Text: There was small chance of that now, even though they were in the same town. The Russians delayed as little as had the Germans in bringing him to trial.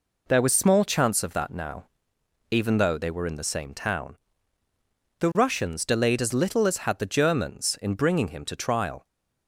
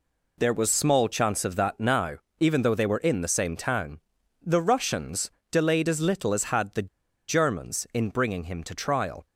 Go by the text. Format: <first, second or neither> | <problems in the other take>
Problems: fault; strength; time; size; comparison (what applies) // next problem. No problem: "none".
first | pauses between "Russians" and "delayed"; slight; at 5.3 s; 0.20 s long // pauses between "the" and "Germans"; at 6.8 s; 0.39 s long